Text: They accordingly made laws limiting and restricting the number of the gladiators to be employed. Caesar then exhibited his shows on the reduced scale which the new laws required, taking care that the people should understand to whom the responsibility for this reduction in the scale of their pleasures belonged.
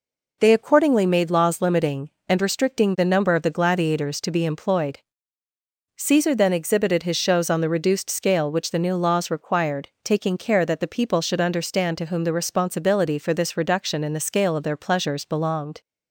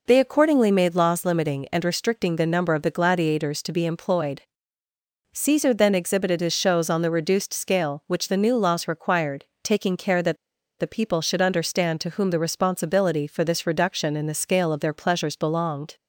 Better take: first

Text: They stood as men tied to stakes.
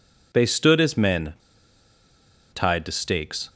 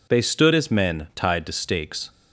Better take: second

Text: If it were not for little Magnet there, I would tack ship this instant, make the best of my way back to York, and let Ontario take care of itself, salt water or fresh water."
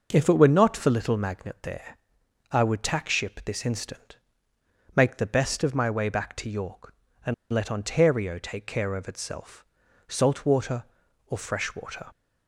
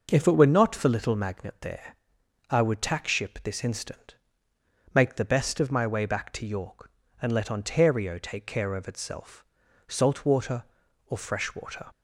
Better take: second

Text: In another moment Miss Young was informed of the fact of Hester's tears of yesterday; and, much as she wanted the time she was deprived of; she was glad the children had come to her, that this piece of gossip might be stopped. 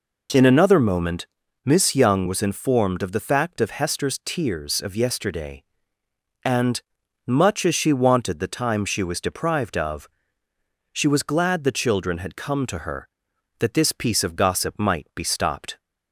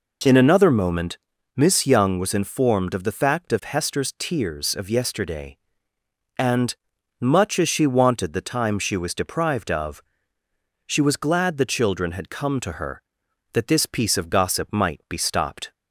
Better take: neither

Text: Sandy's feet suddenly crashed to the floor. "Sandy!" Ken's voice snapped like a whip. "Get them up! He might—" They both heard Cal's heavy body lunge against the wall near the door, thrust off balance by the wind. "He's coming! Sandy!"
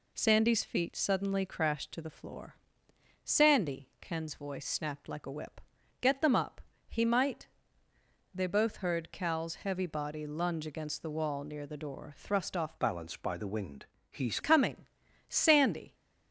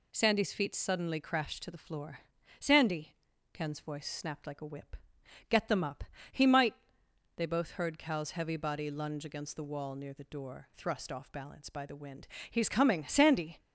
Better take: second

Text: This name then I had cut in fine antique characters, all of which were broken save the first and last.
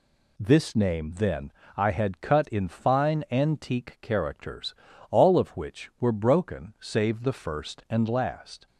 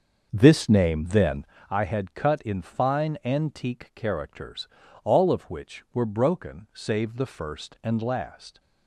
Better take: first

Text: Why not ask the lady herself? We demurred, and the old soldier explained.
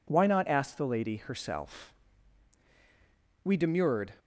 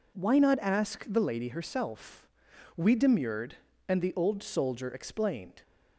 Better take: second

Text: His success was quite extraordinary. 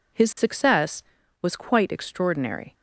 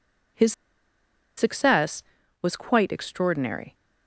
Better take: first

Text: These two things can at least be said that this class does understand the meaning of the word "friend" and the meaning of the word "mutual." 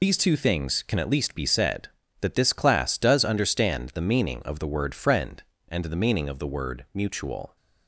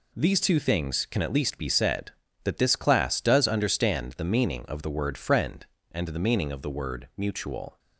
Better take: second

